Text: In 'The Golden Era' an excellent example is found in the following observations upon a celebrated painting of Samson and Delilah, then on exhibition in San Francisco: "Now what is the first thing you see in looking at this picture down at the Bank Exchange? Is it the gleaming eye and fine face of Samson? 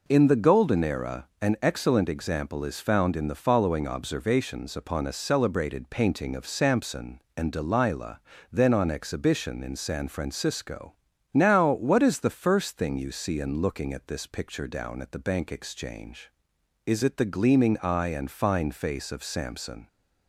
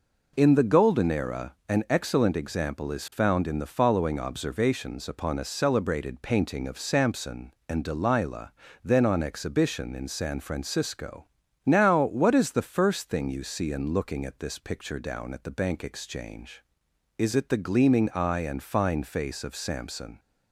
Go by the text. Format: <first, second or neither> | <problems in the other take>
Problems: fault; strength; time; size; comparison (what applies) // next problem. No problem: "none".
neither | pauses between "Era" and "an"; slight; the same in both